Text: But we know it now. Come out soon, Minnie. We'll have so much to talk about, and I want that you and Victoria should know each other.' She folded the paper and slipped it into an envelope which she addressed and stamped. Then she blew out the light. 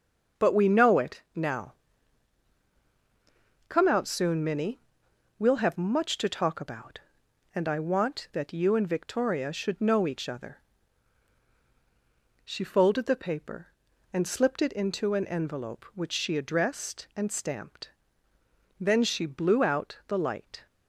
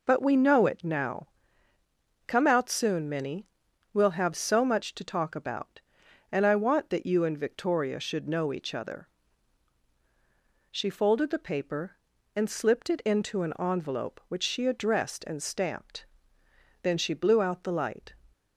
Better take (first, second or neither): second